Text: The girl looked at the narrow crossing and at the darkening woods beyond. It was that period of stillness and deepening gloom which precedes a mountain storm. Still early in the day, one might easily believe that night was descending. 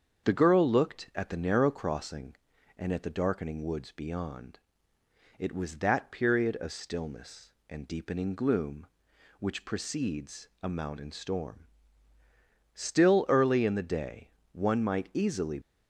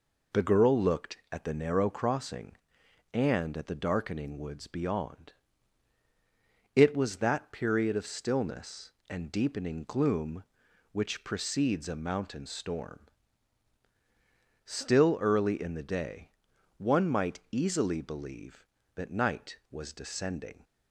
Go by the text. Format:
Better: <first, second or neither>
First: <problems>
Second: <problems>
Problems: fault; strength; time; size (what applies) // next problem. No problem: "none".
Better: second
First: starts louder than the rest; strong; until 1.3 s; 7.5 dB // stops before "believe that night was descending"; at 15.6 s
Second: none